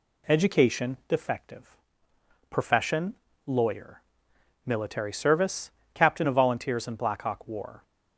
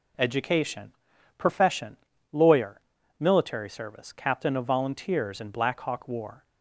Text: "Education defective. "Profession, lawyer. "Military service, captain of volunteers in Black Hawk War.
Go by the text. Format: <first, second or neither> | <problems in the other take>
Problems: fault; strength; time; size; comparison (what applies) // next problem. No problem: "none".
first | skips "defective"; at 1.1 s